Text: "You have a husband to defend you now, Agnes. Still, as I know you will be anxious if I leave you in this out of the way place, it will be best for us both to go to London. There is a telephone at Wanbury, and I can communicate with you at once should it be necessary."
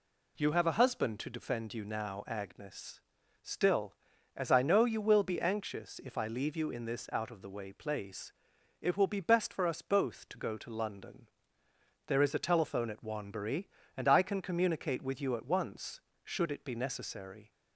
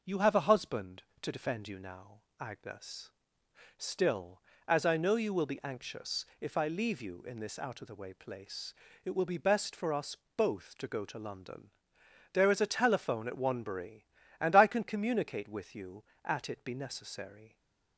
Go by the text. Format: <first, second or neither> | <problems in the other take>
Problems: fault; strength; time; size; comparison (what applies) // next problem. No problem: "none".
first | pauses between "us" and "both"; slight; at 10.1 s; 0.20 s long // skips "once should"; at 16.4 s // stays silent after the last word; slight; from 17.4 s on; 0.5 s long